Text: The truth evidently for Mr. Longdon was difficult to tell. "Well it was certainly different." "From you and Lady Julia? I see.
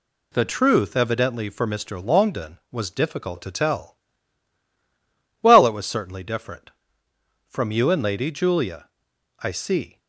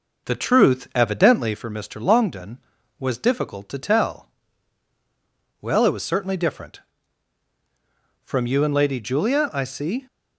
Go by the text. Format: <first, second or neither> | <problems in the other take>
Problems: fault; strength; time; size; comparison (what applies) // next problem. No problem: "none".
first | starts louder than the rest; noticeable; until 1.6 s; 5.5 dB